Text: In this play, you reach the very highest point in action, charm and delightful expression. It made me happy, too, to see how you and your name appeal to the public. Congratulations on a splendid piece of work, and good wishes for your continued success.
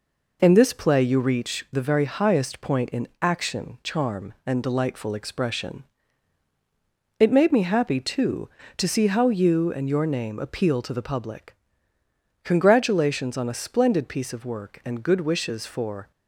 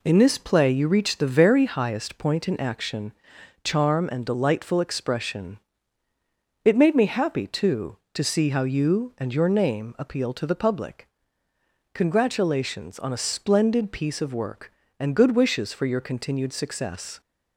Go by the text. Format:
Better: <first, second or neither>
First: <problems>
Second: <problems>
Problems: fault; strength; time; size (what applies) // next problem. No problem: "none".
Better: second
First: stops before "your continued success"; at 16.1 s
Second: none